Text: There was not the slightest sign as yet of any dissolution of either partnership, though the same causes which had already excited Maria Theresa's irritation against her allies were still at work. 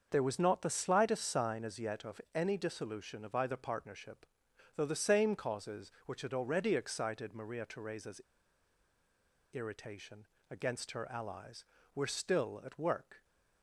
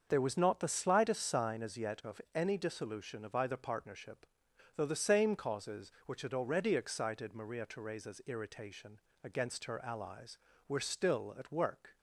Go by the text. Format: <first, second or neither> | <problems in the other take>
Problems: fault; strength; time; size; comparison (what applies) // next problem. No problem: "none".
second | starts louder than the rest; until 1.1 s; 6.5 dB; also in the second // pauses between "Theresa's" and "irritation"; strong; at 8.2 s; 1.3 s long // pauses between "irritation" and "against"; slight; at 10.2 s; 0.22 s long; slight in the second